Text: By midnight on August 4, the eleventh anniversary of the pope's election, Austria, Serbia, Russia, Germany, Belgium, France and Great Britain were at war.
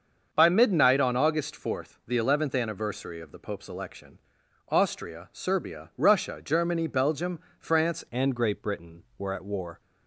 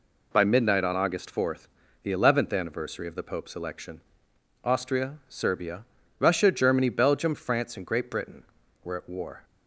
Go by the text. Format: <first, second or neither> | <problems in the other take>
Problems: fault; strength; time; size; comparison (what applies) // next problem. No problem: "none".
second | starts louder than the rest; until 1.3 s; 6.5 dB // changes voice at "and"; from 8.1 s on; 1.7 s long